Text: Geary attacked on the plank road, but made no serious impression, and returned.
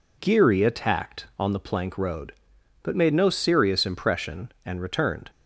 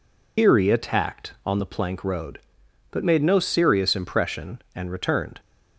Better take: first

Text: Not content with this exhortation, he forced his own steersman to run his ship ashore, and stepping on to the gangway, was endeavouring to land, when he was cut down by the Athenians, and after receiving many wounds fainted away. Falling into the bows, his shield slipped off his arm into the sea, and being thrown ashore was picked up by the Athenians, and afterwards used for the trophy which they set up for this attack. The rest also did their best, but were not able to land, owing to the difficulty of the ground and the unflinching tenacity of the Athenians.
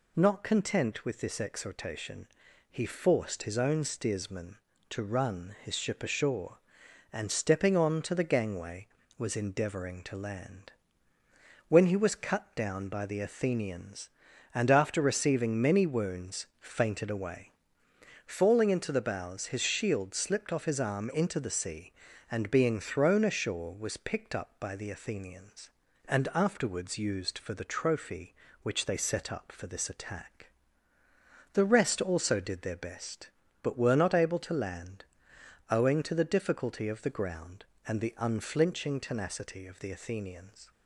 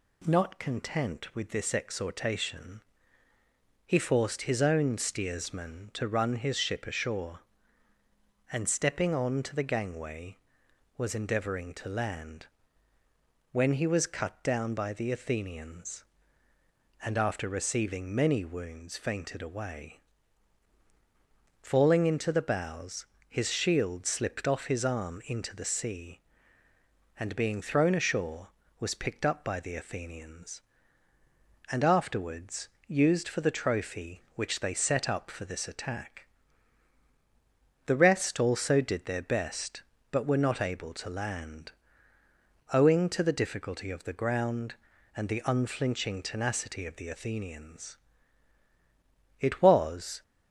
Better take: first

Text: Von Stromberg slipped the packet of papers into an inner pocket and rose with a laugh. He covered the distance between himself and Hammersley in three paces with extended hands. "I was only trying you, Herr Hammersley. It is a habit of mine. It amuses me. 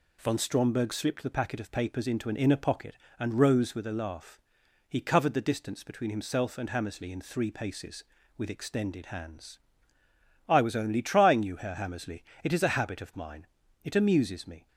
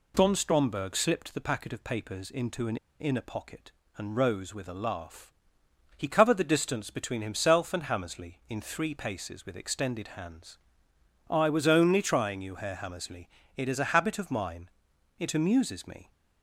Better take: first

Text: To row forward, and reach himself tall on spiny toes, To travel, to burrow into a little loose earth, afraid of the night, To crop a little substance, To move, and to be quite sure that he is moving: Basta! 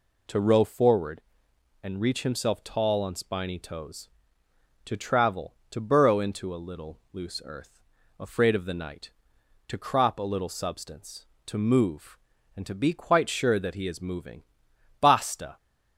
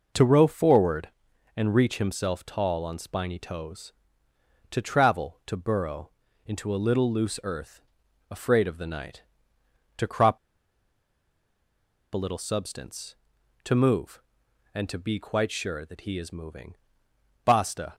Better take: first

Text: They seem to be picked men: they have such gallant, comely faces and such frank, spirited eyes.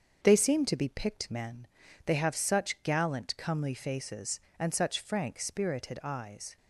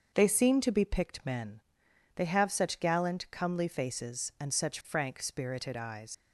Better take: first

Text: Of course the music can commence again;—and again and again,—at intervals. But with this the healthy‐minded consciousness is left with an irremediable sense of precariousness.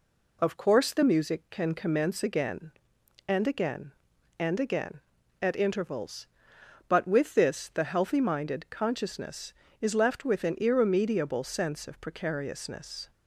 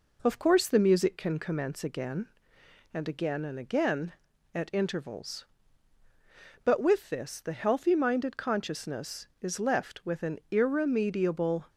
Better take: first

